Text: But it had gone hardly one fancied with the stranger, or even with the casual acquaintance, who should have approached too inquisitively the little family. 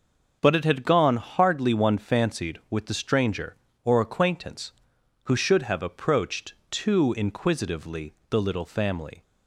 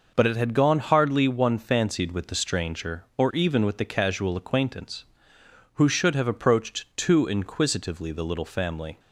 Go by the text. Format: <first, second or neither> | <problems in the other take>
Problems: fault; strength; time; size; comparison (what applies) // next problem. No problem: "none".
second | starts louder than the rest; noticeable; until 1.4 s; 6 dB // skips "even with the casual"; at 3.9 s // pauses between "approached" and "too"; slight; at 6.5 s; 0.16 s long // pauses between "inquisitively" and "the"; slight; at 8.1 s; 0.16 s long